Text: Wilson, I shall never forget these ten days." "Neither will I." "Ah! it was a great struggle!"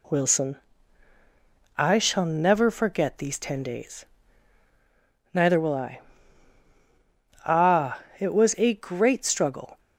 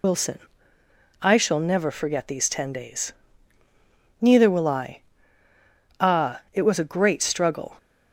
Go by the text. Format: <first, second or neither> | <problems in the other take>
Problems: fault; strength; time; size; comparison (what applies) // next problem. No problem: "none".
first | loses the start of "Wilson"; at 0.0 s; 70 ms